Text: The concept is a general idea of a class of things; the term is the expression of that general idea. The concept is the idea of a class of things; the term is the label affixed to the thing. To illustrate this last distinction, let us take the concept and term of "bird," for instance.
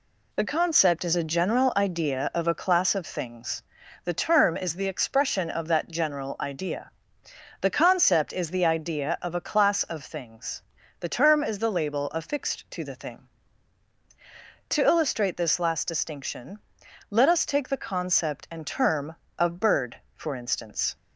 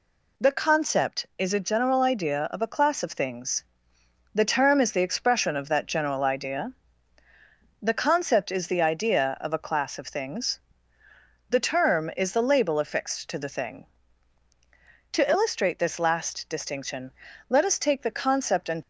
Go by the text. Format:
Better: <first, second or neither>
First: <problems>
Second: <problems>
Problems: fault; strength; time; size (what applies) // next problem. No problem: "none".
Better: first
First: none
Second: stops before "term of bird for instance"; at 18.8 s